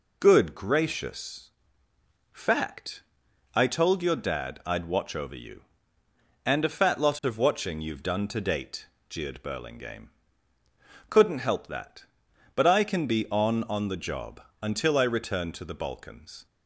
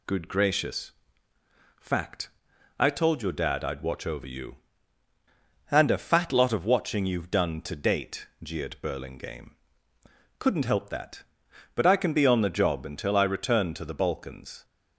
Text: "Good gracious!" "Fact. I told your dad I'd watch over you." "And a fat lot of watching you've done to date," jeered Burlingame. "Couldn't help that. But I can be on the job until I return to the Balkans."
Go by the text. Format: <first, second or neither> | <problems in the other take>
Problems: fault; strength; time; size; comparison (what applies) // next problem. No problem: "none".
second | says "on" twice; at 13.6 s // pauses between "job" and "until"; slight; at 14.3 s; 0.22 s long